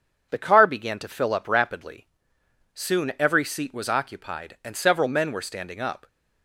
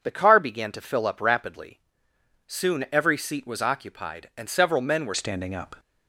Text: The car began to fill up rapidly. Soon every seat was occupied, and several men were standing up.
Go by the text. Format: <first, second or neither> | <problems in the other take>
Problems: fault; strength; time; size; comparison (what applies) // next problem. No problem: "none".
first | changes voice at "standing"; from 5.1 s on; 0.6 s long